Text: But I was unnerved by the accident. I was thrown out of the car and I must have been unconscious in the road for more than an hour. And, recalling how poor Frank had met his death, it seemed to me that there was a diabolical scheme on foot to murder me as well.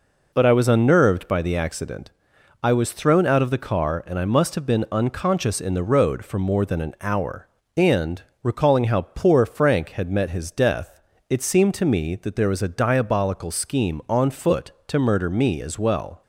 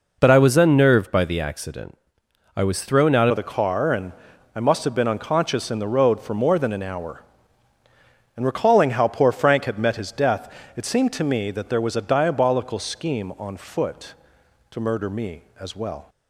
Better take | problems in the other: first | changes voice at "of"; from 3.3 s on; 12.7 s long // pauses between "and" and "I"; at 4.1 s; 0.44 s long

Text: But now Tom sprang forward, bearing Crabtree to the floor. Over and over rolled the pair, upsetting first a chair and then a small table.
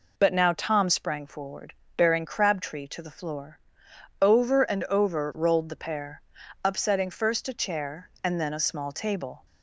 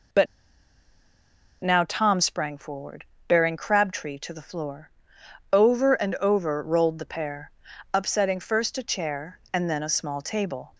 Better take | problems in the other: first | pauses between "But" and "now"; strong; at 0.2 s; 1.3 s long

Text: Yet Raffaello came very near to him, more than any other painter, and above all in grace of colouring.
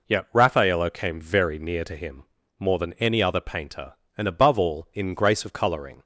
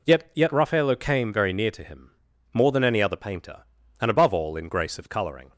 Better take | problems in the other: first | says "Yet" twice; at 0.3 s

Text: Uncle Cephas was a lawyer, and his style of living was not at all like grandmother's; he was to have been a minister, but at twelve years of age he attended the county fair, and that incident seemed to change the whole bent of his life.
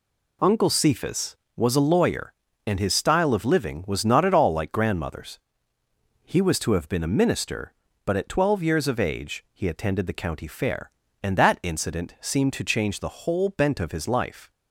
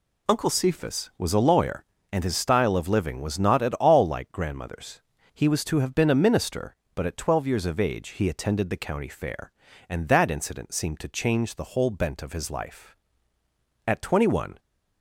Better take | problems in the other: first | goes on to say "At twenty one"; noticeable; from 13.8 s on; 0.74 s long

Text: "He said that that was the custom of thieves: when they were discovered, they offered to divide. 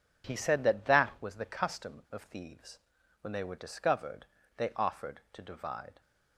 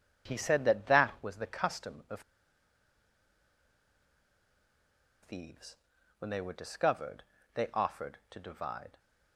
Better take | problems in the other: first | pauses between "of" and "thieves"; strong; at 2.2 s; 3.0 s long

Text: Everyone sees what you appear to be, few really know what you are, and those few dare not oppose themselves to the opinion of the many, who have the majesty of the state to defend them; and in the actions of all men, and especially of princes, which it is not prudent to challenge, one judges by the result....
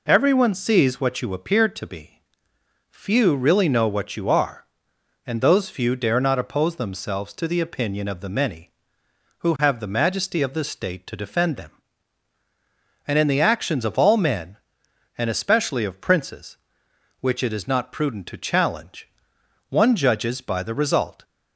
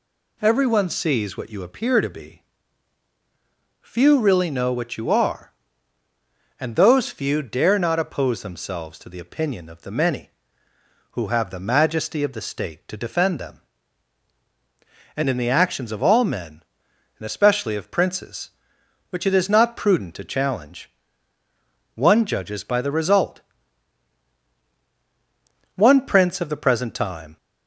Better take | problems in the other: first | goes on to say "One prince of the present time"; from 25.7 s on; 1.6 s long

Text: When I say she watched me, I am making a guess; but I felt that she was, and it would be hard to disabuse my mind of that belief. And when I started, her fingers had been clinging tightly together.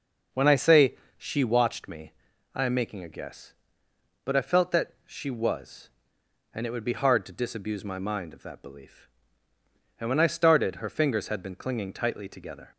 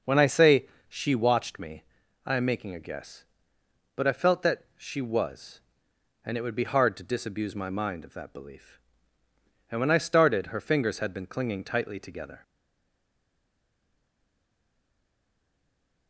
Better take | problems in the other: first | pauses between "say" and "she"; slight; at 0.6 s; 0.22 s long; slight in the first // stays silent after the last word; strong; from 12.4 s on; 3.6 s long

